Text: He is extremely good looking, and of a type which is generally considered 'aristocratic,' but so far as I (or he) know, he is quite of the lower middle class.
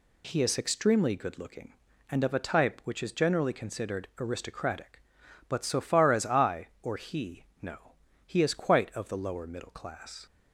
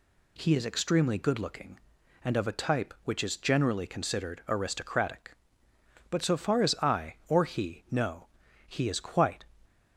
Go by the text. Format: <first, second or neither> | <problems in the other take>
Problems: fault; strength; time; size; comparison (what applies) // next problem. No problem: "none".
first | stops before "of the lower middle class"; at 9.6 s